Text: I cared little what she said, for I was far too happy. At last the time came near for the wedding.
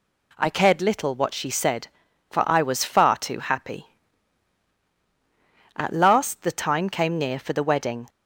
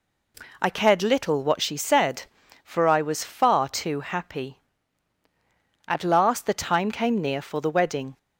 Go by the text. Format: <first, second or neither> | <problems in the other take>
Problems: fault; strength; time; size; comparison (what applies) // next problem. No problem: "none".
neither | none